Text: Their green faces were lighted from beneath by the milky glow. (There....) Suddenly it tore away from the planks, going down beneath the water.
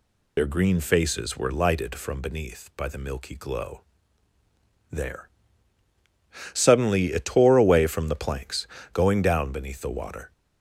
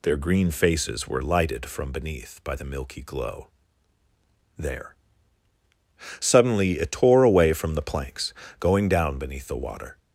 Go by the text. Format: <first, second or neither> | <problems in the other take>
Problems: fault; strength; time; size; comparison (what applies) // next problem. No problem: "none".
second | loses the start of "Their"; at 0.3 s; 45 ms